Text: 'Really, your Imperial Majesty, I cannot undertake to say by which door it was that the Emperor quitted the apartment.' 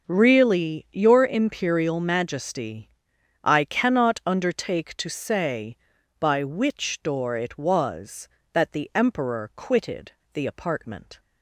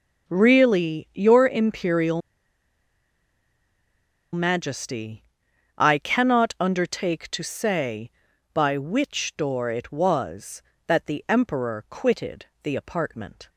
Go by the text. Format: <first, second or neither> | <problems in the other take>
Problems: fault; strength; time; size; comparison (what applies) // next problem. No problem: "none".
first | pauses between "Imperial" and "Majesty"; strong; at 2.2 s; 2.1 s long // pauses between "quitted" and "the"; slight; at 12.4 s; 0.16 s long; slight in the first